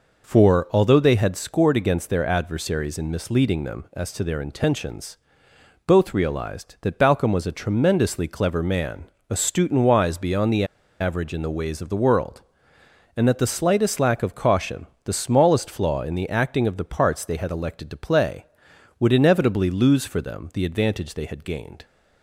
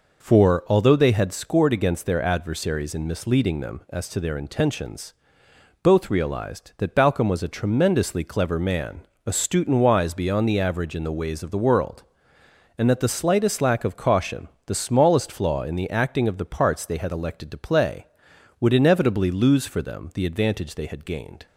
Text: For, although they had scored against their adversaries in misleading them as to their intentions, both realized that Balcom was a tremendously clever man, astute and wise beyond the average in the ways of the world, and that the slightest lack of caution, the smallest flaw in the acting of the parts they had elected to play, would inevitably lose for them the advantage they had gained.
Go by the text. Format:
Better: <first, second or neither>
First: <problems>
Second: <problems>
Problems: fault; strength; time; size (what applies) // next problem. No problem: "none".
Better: second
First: pauses between "the" and "average"; slight; at 10.6 s; 0.35 s long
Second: none